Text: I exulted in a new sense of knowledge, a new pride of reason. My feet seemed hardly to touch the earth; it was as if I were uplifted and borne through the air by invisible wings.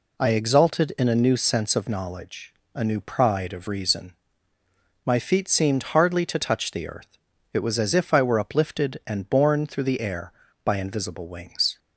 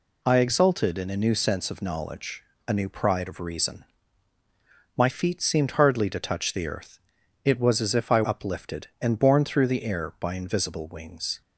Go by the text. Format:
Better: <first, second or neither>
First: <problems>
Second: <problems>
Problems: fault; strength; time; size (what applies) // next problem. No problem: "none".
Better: first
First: none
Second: skips "were"; at 8.2 s